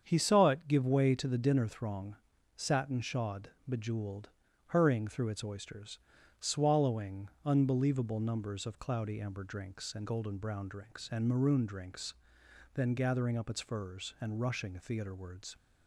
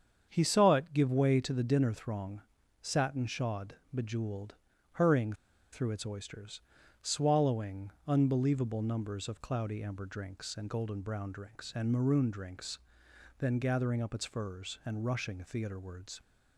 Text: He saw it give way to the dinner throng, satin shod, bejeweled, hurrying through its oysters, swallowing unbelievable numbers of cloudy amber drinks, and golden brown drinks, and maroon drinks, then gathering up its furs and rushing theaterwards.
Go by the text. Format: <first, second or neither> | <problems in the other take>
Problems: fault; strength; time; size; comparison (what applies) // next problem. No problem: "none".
first | starts louder than the rest; strong; until 1.3 s; 7.5 dB; strong in the first // pauses between "hurrying" and "through"; at 5.3 s; 0.39 s long // pauses between "swallowing" and "unbelievable"; slight; at 7.9 s; 0.16 s long; slight in the first